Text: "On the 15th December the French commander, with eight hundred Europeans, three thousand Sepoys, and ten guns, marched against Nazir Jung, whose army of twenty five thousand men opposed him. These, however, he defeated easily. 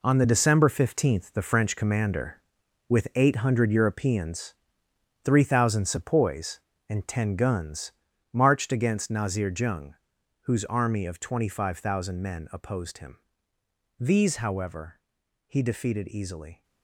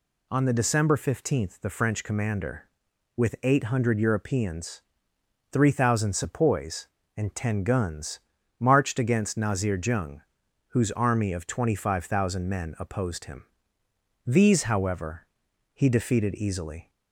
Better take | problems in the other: second | gets quieter; strong; throughout; 10 dB

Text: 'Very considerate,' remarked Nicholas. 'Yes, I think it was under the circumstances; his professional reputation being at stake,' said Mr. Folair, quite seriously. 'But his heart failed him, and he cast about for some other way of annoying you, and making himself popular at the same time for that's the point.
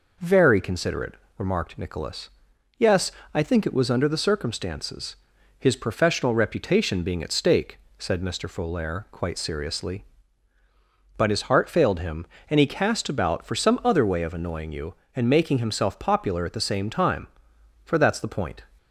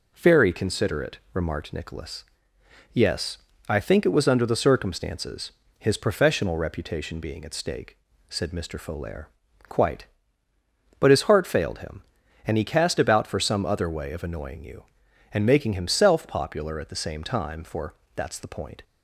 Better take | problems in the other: first | skips "seriously"; at 10.5 s // pauses between "for" and "that's"; slight; at 17.9 s; 0.20 s long

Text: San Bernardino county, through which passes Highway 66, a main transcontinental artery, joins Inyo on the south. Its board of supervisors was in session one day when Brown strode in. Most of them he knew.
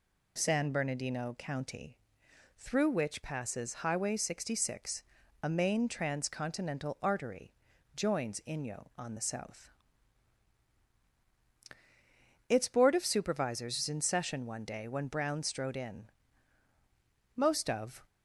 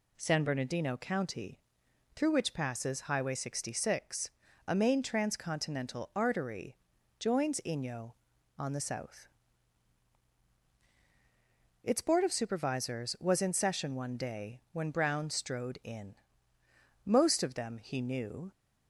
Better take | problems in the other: second | stops before "them he knew"; at 18.0 s

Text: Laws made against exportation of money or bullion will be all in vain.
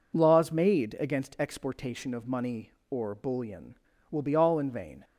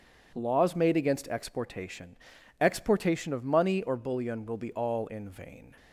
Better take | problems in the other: first | says "exportation" twice; at 2.5 s

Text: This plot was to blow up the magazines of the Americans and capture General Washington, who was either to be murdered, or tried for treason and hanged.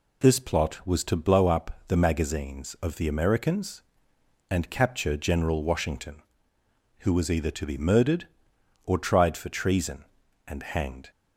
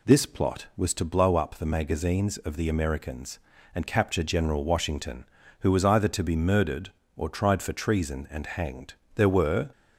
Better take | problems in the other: first | goes on to say "There were"; from 9.1 s on; 0.56 s long

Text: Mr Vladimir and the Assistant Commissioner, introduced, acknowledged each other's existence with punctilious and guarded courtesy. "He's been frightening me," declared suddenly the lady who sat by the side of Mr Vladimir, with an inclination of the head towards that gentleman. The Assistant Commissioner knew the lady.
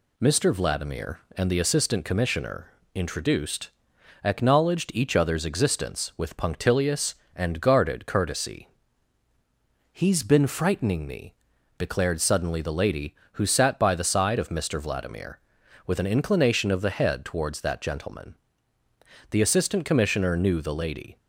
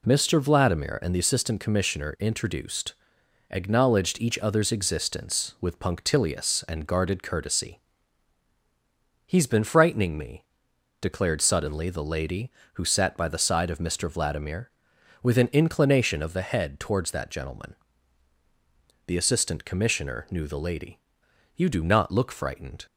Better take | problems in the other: first | goes on to say "You do not look frightened"; noticeable; from 21.5 s on; 1.3 s long

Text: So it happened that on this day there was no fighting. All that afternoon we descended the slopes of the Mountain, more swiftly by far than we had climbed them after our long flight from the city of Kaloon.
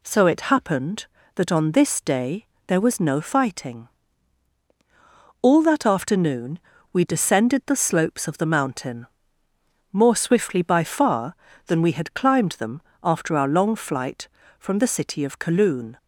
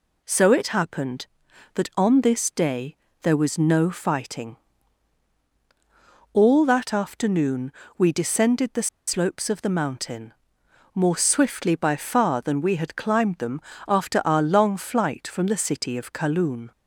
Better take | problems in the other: first | pauses between "day" and "there"; slight; at 2.9 s; 0.28 s long; slight in the first // pauses between "afternoon" and "we"; slight; at 7.7 s; 0.24 s long; slight in the first // pauses between "the" and "slopes"; slight; at 8.8 s; 0.18 s long // pauses between "them" and "after"; slight; at 13.6 s; 0.26 s long; slight in the first

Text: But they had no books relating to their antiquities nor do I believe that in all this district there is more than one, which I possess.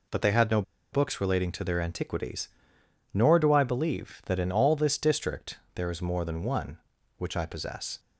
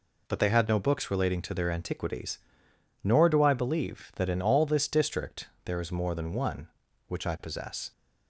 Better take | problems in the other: second | pauses between "no" and "books"; slight; at 0.6 s; 0.30 s long // pauses between "antiquities" and "nor"; noticeable; at 2.4 s; 0.66 s long; noticeable in the second // pauses between "district" and "there"; slight; at 5.5 s; 0.20 s long; slight in the second

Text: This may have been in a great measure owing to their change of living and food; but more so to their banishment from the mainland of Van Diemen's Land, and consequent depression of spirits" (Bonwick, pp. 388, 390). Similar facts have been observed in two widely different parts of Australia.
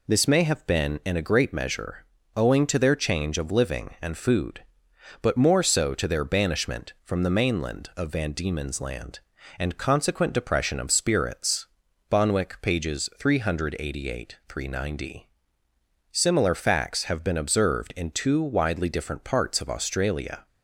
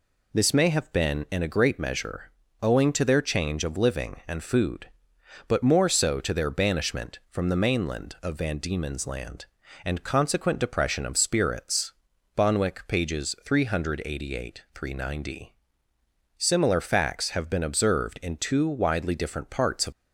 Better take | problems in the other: first | pauses between "measure" and "owing"; slight; at 2.2 s; 0.30 s long; slight in the first // stops before "Australia"; at 19.9 s

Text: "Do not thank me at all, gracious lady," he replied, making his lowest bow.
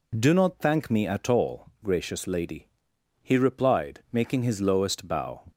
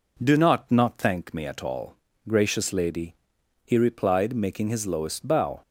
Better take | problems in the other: first | says "not" twice; at 0.7 s

